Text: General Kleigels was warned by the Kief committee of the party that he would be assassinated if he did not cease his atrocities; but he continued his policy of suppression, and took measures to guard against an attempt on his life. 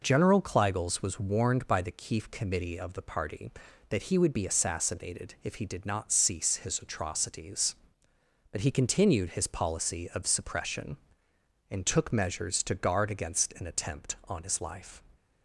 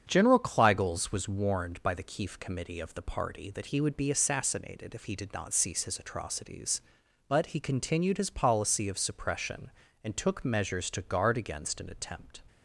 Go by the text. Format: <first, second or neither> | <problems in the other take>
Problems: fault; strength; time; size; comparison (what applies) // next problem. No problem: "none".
first | starts louder than the rest; strong; until 1.0 s; 8 dB // stops before "on his life"; at 12.4 s